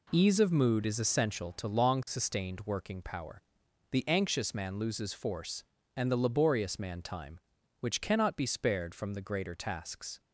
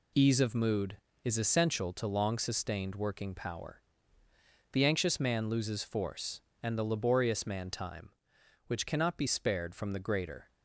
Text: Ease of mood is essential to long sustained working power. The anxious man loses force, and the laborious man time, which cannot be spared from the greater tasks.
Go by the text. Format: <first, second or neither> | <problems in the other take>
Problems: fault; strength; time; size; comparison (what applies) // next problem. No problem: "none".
first | stops before "tasks"; at 10.5 s